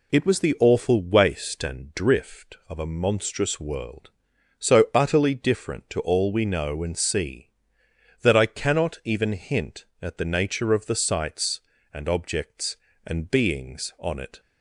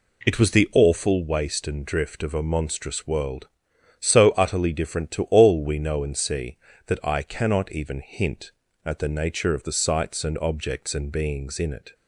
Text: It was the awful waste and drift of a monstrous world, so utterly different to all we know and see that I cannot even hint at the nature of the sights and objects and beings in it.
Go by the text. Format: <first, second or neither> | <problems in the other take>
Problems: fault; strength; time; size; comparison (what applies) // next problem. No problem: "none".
second | says "on" for "in"; at 13.9 s